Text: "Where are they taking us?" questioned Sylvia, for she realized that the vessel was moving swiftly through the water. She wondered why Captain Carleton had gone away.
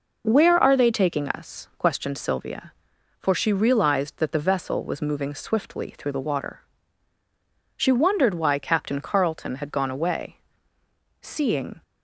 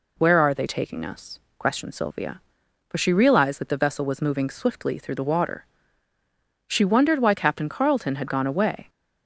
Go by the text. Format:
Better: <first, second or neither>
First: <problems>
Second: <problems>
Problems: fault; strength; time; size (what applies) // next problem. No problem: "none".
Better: second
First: goes on to say "Seeing"; noticeable; from 11.2 s on; 0.62 s long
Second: none